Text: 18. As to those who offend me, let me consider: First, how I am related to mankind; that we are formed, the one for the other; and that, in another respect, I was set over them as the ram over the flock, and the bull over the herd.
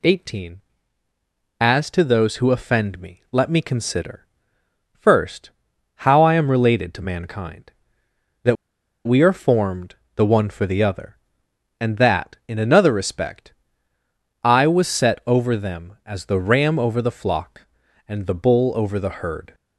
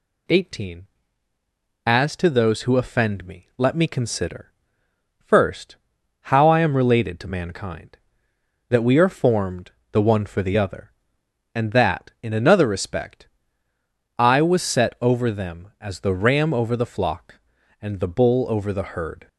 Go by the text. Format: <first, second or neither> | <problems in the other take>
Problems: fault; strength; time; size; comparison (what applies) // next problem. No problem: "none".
second | pauses between "that" and "we"; noticeable; at 8.5 s; 0.50 s long